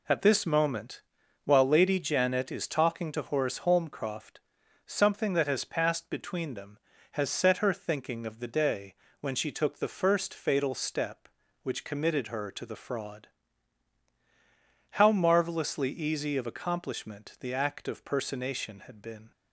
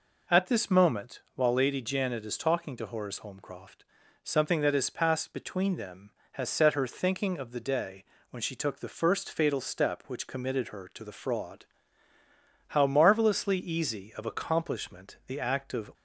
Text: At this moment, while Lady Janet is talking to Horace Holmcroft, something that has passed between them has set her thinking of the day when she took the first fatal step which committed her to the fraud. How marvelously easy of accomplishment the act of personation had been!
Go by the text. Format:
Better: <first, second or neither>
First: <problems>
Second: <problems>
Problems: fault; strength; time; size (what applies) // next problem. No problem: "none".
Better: first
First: pauses between "day" and "when"; slight; at 8.9 s; 0.26 s long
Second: pauses between "day" and "when"; slight; at 8.0 s; 0.26 s long // stops before "personation had been"; at 15.9 s